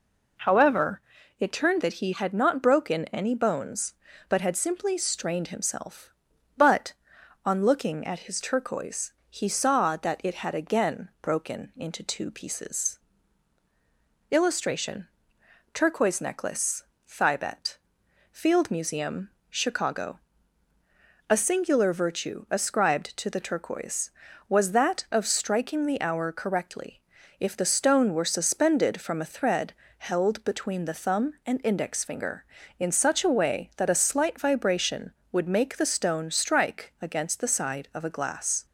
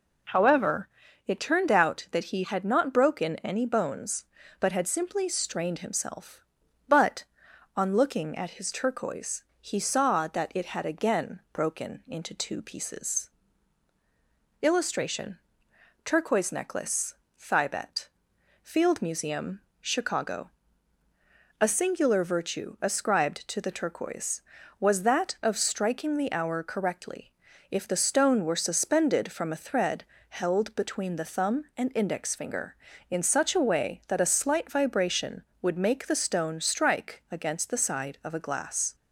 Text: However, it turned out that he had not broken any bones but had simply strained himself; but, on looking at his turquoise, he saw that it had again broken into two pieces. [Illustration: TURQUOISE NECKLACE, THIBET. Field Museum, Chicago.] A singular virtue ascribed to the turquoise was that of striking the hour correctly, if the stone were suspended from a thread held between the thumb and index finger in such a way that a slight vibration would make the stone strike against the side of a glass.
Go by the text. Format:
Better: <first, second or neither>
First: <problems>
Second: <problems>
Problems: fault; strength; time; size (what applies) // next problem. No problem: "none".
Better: second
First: skips "out"; at 1.8 s // pauses between "thread" and "held"; slight; at 29.7 s; 0.26 s long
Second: pauses between "thread" and "held"; slight; at 30.0 s; 0.26 s long